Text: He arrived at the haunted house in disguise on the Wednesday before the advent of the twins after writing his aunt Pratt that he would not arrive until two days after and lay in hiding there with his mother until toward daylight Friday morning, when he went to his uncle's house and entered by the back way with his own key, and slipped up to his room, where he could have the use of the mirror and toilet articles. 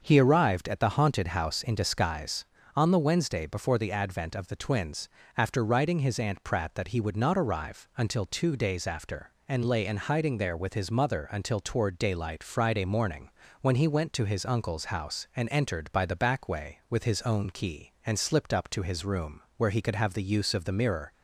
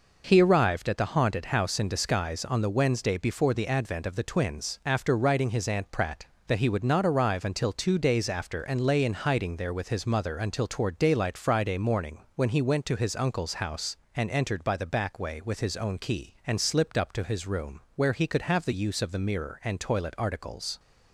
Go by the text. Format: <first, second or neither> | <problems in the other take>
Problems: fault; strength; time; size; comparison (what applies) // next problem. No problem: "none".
second | starts louder than the rest; until 1.0 s; 6.5 dB // pauses between "twins" and "after"; slight; at 5.0 s; 0.28 s long // stops before "and toilet articles"; at 21.1 s